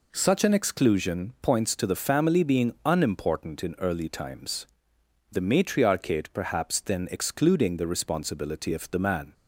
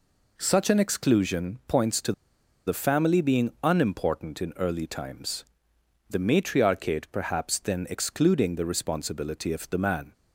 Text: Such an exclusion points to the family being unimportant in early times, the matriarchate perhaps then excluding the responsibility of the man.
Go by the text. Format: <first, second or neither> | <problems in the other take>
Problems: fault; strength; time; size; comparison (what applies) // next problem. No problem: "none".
first | pauses between "to" and "the"; noticeable; at 2.1 s; 0.54 s long